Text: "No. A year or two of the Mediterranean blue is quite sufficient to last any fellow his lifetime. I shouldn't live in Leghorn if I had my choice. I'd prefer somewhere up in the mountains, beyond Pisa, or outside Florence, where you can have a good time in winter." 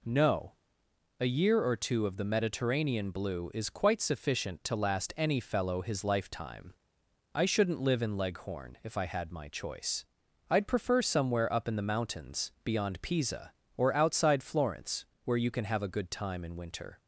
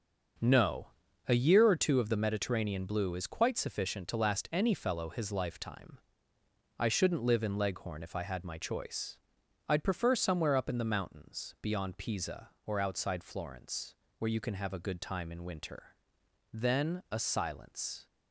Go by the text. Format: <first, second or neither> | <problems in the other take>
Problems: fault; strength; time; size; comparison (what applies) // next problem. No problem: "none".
first | starts louder than the rest; until 1.8 s; 6.5 dB // goes on to say "Then a silence"; from 16.5 s on; 1.5 s long